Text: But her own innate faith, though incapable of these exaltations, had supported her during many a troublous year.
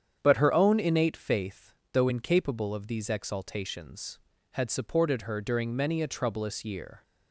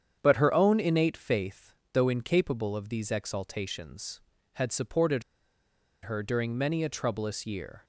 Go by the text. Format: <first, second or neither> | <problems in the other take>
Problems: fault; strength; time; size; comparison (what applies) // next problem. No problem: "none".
first | starts louder than the rest; strong; until 1.2 s; 8.5 dB; strong in the first // pauses between "supported" and "her"; noticeable; at 5.2 s; 0.81 s long